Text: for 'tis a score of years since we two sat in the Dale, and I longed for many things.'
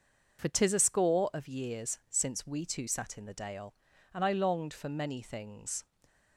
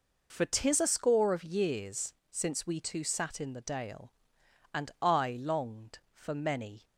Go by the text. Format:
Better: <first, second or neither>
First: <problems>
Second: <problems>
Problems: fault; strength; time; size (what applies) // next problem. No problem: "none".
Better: first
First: none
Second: pauses between "years" and "since"; slight; at 2.1 s; 0.18 s long // stops before "things"; at 6.8 s